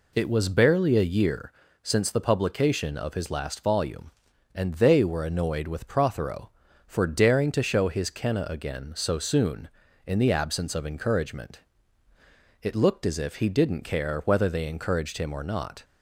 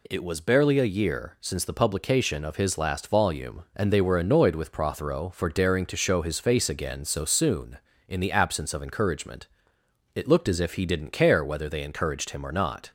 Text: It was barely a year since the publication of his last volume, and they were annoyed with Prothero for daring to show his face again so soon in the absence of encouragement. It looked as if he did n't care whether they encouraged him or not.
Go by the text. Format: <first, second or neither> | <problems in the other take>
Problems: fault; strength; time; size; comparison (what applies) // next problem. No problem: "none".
second | pauses between "year" and "since"; slight; at 1.5 s; 0.32 s long // says "kenna" for "face"; at 8.1 s